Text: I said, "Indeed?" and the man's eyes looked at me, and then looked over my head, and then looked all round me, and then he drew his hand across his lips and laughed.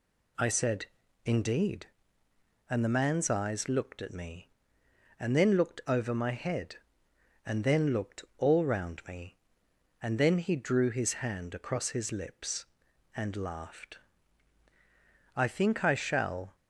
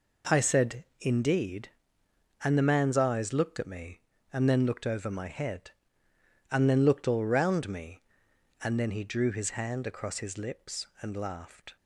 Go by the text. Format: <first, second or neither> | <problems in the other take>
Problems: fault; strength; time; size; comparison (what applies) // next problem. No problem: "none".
second | goes on to say "I think I shall"; noticeable; from 15.3 s on; 1.2 s long